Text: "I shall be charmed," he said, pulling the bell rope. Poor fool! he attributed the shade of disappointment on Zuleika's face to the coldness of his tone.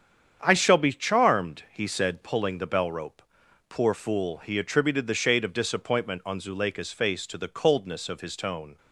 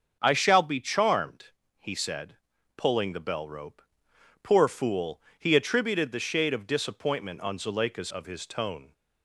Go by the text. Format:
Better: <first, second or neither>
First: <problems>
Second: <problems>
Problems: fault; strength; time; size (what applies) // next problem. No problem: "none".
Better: first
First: starts louder than the rest; strong; until 1.4 s; 8 dB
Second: starts louder than the rest; until 1.2 s; 6.5 dB // skips "face to the coldness"; at 8.1 s